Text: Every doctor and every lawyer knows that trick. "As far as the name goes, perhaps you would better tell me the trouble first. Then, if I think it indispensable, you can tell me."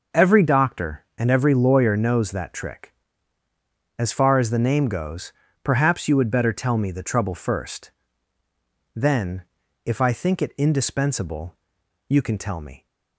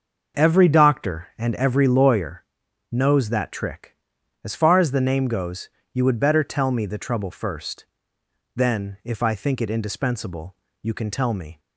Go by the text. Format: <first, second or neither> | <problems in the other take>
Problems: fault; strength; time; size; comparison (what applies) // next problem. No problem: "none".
first | starts louder than the rest; noticeable; until 1.4 s; 6 dB // pauses between "lawyer" and "knows"; noticeable; at 2.4 s; 0.48 s long // skips "perhaps"; at 5.8 s